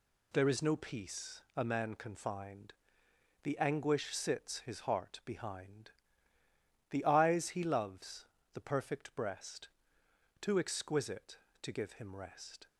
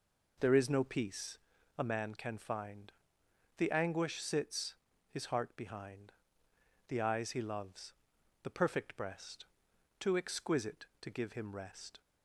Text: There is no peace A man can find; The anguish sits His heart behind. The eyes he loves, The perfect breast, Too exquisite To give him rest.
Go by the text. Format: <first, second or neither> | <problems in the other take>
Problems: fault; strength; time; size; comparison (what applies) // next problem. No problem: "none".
first | starts louder than the rest; noticeable; until 1.5 s; 4.5 dB // pauses between "peace" and "A"; at 1.3 s; 0.40 s long // pauses between "sits" and "His"; slight; at 4.7 s; 0.34 s long